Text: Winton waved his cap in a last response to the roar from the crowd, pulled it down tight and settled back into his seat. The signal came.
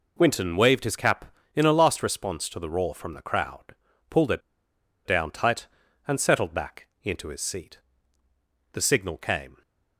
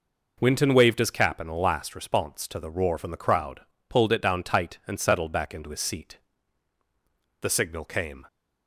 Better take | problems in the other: second | pauses between "it" and "down"; noticeable; at 4.4 s; 0.64 s long // pauses between "back" and "into"; slight; at 6.8 s; 0.16 s long

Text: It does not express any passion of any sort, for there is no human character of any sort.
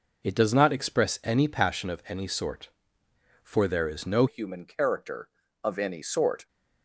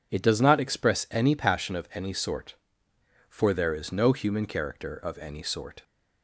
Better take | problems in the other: second | changes voice at "human"; from 4.2 s on; 2.2 s long

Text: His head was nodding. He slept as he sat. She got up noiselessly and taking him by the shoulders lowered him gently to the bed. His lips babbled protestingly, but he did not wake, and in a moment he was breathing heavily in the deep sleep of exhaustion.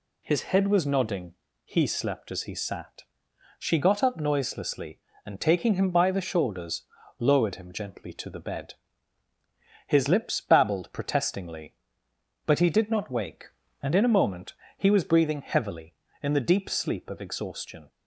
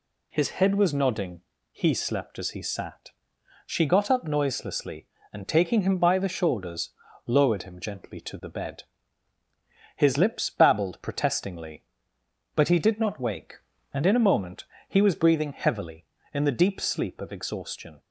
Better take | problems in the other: neither | pauses between "shoulders" and "lowered"; the same in both // pauses between "moment" and "he"; slight; the same in both

